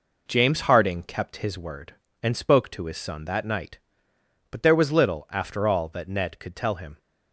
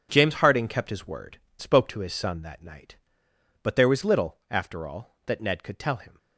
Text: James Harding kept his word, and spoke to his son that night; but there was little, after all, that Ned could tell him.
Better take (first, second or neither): first